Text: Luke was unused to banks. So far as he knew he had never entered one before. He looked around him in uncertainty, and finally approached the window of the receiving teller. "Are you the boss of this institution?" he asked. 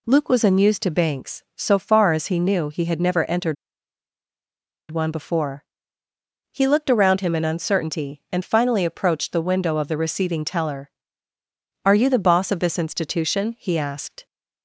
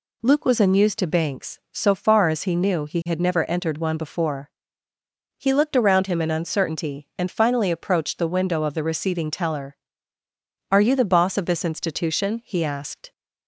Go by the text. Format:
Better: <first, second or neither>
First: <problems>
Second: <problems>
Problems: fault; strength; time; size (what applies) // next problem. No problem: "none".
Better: second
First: pauses between "entered" and "one"; strong; at 3.5 s; 1.3 s long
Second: none